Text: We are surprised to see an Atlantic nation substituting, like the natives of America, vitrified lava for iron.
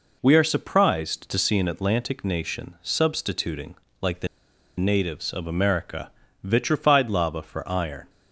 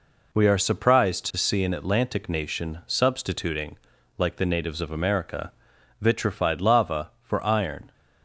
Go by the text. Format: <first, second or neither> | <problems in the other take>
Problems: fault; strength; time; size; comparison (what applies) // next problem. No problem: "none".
second | pauses between "the" and "natives"; noticeable; at 4.2 s; 0.50 s long